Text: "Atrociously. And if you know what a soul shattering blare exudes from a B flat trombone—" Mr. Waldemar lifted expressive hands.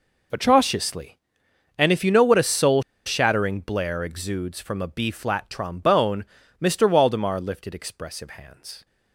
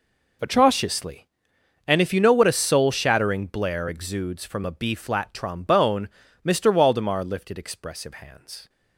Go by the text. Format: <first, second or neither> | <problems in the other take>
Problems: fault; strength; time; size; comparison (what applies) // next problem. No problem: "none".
second | pauses between "soul" and "shattering"; slight; at 2.8 s; 0.23 s long